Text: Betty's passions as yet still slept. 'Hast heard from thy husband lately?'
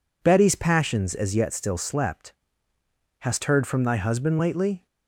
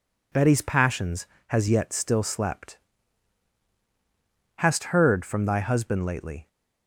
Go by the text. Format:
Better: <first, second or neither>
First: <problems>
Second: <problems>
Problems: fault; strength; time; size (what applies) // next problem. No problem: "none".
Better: first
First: none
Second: says "has" for "as"; at 1.4 s